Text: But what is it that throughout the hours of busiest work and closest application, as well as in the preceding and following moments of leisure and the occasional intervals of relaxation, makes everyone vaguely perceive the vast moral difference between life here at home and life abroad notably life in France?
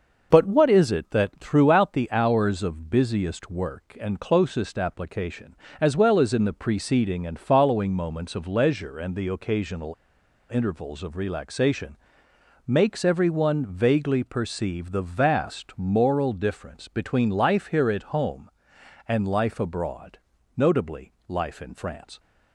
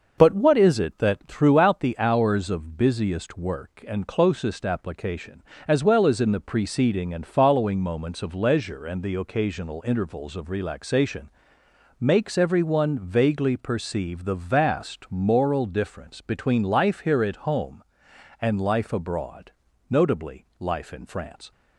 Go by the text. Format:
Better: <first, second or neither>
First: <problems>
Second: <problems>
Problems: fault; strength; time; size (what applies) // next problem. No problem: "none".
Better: second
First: starts louder than the rest; noticeable; until 1.3 s; 6 dB // pauses between "occasional" and "intervals"; noticeable; at 9.9 s; 0.60 s long // pauses between "abroad" and "notably"; at 20.1 s; 0.38 s long // pauses between "notably" and "life"; slight; at 21.1 s; 0.16 s long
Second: starts louder than the rest; noticeable; until 1.1 s; 6 dB // pauses between "abroad" and "notably"; at 19.5 s; 0.38 s long